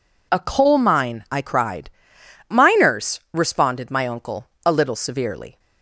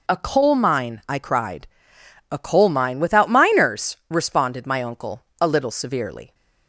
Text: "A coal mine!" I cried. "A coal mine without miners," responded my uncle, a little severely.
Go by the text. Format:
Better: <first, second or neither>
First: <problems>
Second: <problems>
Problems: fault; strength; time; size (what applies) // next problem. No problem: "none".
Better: second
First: skips "A coal mine without"; at 2.2 s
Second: none